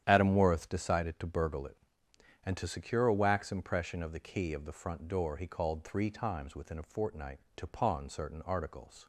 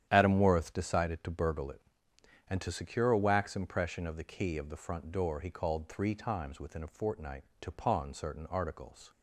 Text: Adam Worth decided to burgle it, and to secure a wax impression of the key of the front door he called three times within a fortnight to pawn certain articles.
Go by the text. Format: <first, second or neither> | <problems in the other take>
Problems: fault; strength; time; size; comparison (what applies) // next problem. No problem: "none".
neither | starts louder than the rest; strong; the same in both